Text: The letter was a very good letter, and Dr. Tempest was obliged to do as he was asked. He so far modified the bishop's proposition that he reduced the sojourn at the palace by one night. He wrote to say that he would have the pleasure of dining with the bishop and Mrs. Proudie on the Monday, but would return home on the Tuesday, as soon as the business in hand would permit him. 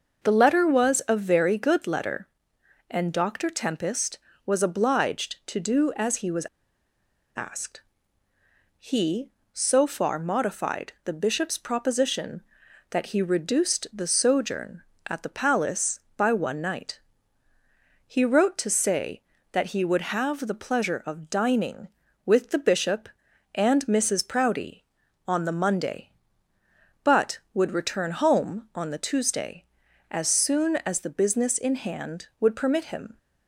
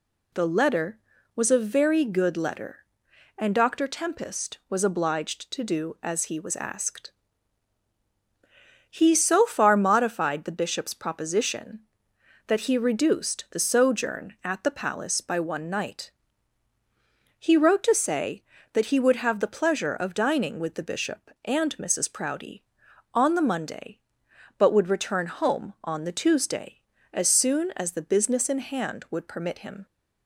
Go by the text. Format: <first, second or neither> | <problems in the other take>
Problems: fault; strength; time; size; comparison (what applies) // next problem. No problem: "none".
second | pauses between "was" and "asked"; noticeable; at 6.4 s; 0.88 s long